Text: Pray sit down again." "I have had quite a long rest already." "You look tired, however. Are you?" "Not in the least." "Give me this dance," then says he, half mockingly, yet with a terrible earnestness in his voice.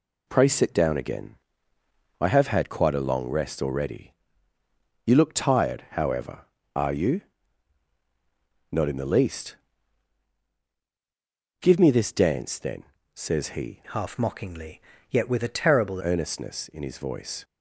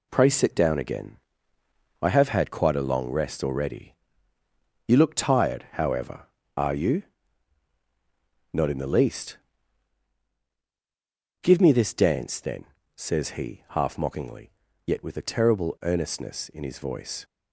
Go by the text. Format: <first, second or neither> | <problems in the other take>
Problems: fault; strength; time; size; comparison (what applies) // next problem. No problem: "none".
second | pauses between "then" and "says"; slight; at 12.8 s; 0.30 s long; slight in the second // changes voice from "half" to "terrible"; from 13.9 to 16.0 s; 2.1 s long